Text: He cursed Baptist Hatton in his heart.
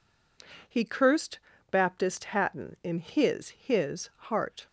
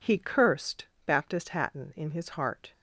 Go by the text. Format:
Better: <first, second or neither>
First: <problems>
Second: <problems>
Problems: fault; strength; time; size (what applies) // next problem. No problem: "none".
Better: second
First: pauses between "cursed" and "Baptist"; slight; at 1.3 s; 0.32 s long // says "his" twice; at 3.5 s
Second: pauses between "cursed" and "Baptist"; slight; at 0.8 s; 0.20 s long